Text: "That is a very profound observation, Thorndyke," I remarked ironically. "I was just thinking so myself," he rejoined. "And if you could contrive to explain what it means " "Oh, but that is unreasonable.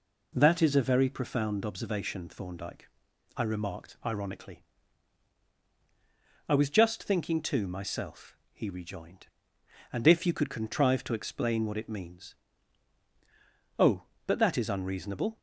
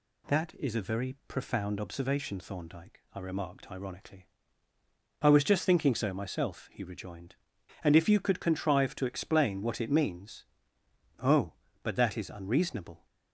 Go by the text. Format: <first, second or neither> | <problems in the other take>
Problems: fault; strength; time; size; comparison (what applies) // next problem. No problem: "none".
second | says "too" for "so"; at 7.3 s